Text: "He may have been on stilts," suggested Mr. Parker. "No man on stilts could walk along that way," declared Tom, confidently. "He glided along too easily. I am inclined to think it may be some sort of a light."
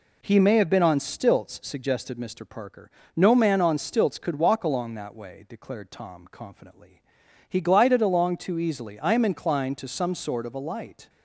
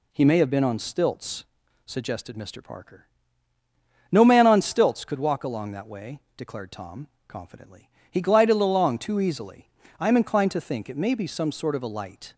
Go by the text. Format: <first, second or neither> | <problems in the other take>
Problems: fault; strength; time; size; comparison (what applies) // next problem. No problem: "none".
second | skips "think it may be"; at 9.8 s